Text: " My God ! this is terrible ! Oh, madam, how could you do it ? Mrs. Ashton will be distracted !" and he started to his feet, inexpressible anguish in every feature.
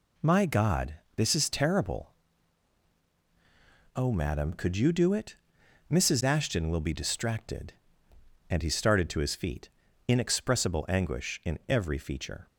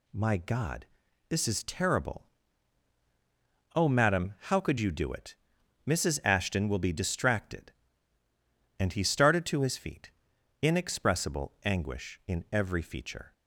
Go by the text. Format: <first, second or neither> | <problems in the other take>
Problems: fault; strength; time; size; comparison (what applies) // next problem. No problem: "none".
second | skips "how"; at 4.5 s